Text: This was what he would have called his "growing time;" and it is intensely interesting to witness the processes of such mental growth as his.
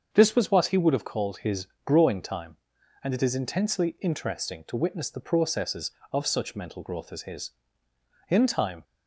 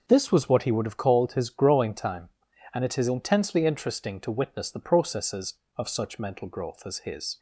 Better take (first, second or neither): second